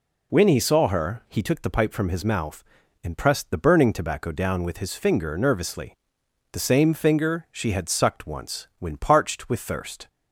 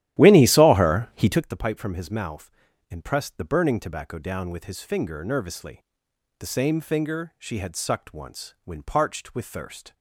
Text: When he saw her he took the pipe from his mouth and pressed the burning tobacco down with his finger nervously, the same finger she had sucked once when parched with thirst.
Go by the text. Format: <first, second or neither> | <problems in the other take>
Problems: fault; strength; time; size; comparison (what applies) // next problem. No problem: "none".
first | starts louder than the rest; strong; until 1.5 s; 13 dB